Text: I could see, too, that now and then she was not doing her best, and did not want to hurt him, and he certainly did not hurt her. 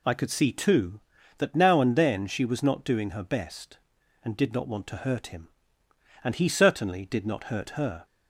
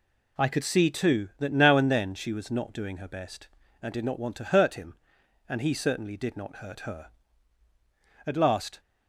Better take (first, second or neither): first